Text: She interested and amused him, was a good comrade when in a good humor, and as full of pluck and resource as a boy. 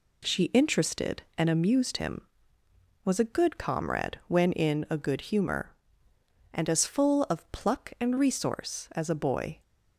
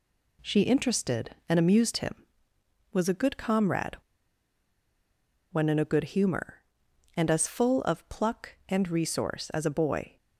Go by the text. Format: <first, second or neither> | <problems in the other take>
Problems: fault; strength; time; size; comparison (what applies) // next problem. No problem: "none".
first | pauses between "comrade" and "when"; strong; at 3.9 s; 1.5 s long